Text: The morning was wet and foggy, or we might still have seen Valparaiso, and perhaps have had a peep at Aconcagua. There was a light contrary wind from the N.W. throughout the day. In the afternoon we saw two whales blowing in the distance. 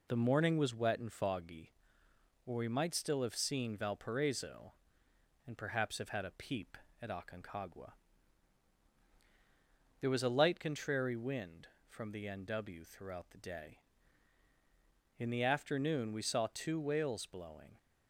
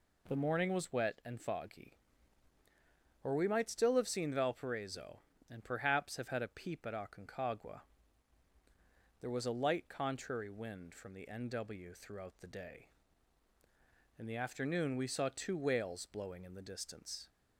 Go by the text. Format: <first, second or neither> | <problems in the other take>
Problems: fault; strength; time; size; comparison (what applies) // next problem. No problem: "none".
second | stops before "in the distance"; at 17.7 s